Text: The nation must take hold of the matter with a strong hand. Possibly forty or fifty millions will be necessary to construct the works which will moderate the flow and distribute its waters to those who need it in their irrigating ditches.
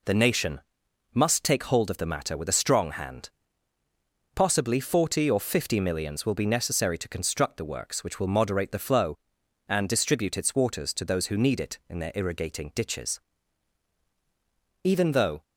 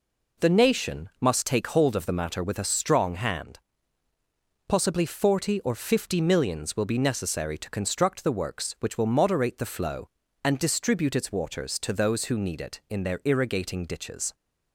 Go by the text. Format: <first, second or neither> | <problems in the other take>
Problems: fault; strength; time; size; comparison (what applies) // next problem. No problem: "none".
second | pauses between "nation" and "must"; noticeable; at 0.6 s; 0.52 s long // goes on to say "Even though"; from 14.8 s on; 0.60 s long